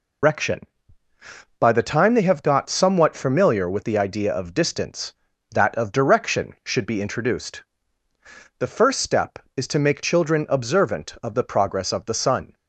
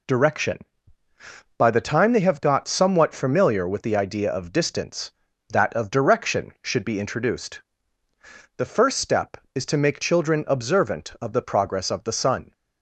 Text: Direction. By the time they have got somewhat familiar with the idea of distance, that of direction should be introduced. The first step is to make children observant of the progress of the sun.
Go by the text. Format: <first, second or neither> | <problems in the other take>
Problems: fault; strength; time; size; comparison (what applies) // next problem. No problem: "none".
second | loses the start of "Direction"; at 0.2 s; 150 ms